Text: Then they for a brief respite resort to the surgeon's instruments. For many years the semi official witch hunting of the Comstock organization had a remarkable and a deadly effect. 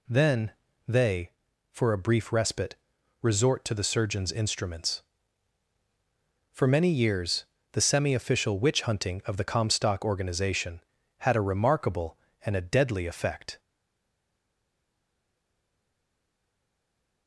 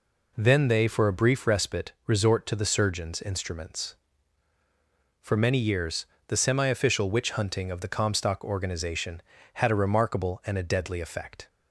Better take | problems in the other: second | pauses between "Then" and "they"; slight; at 0.5 s; 0.36 s long // pauses between "respite" and "resort"; noticeable; at 2.7 s; 0.46 s long; slight in the second // pauses between "years" and "the"; slight; at 7.4 s; 0.28 s long; slight in the second // stays silent after the last word; strong; from 13.5 s on; 3.7 s long

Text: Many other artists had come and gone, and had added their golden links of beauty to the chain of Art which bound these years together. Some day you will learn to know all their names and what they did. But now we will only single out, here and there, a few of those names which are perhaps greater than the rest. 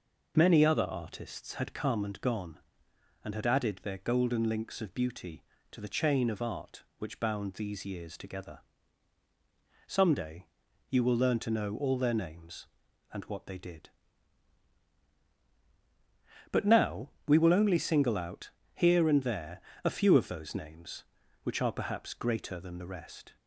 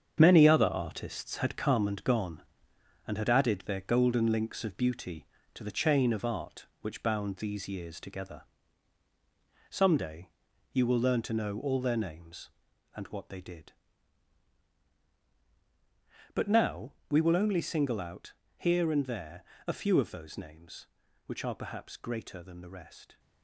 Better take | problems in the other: first | gets quieter; strong; throughout; 8 dB // pauses between "day" and "you"; at 10.3 s; 0.42 s long; also in the first // pauses between "now" and "we"; slight; at 16.9 s; 0.18 s long; slight in the first

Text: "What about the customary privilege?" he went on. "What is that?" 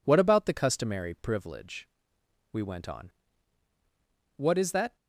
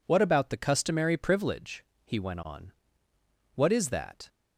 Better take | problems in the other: second | says "we" for "he"; at 2.5 s

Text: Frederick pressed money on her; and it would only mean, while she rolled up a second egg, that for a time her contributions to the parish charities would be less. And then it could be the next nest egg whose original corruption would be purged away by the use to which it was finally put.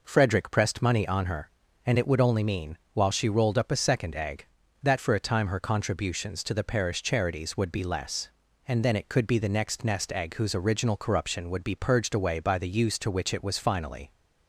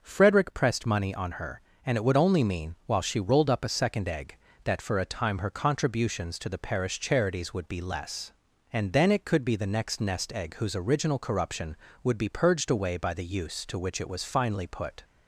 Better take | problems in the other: second | stops before "put"; at 14.1 s

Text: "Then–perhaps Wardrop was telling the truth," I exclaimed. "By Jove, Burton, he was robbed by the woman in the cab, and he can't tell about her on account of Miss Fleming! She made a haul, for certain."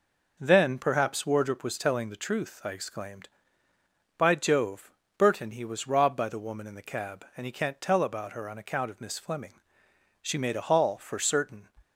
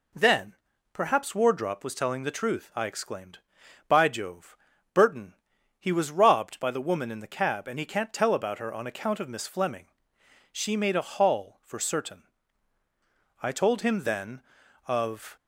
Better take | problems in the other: first | goes on to say "I told him then of"; strong; from 13.4 s on; 1.9 s long

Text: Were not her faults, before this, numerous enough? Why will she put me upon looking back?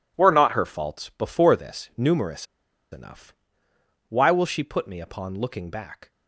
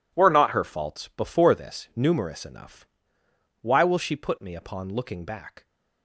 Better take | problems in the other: second | pauses between "numerous" and "enough"; noticeable; at 2.4 s; 0.46 s long

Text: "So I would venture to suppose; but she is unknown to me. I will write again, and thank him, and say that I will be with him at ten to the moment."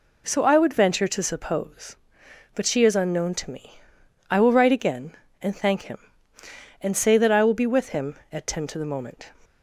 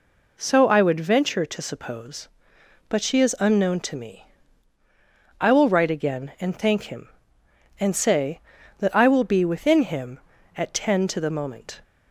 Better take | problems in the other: first | says "within" for "with"; at 9.4 s

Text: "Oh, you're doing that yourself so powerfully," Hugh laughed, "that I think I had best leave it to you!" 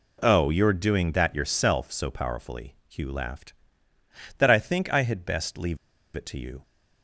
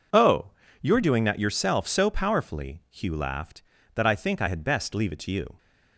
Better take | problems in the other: second | pauses between "leave" and "it"; at 5.7 s; 0.39 s long

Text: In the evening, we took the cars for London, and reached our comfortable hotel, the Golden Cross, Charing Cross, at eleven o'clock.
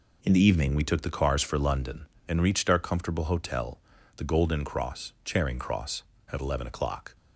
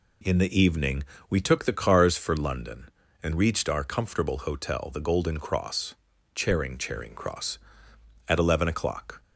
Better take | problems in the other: first | says "Charing" twice; at 6.7 s

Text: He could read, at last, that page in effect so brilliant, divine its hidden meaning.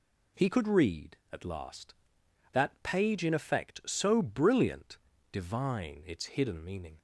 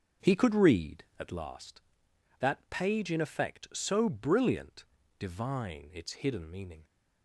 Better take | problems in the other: first | starts louder than the rest; until 1.5 s; 6.5 dB

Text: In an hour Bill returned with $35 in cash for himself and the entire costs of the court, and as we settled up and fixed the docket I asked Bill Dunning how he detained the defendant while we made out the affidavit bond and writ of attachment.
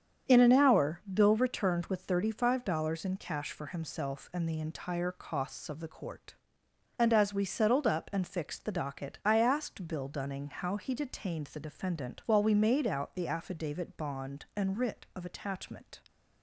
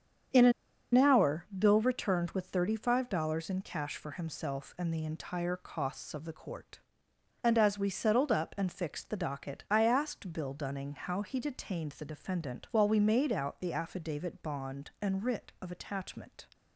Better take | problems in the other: first | starts louder than the rest; strong; until 1.8 s; 8 dB; strong in the first // pauses between "an" and "hour"; at 0.5 s; 0.43 s long

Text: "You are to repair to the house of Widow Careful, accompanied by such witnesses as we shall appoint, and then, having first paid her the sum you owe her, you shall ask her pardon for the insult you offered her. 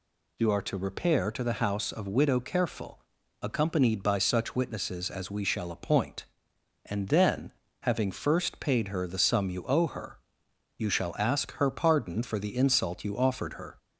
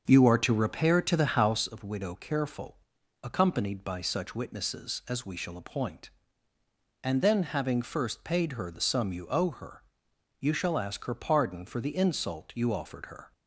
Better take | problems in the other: first | starts louder than the rest; until 1.7 s; 6.5 dB

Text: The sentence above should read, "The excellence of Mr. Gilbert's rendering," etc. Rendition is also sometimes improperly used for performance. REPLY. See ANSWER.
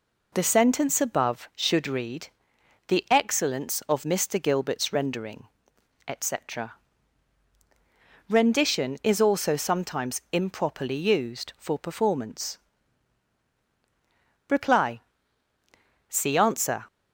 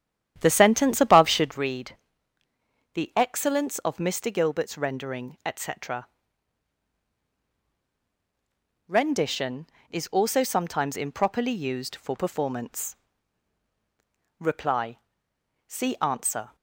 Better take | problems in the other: first | starts louder than the rest; strong; until 1.7 s; 10 dB

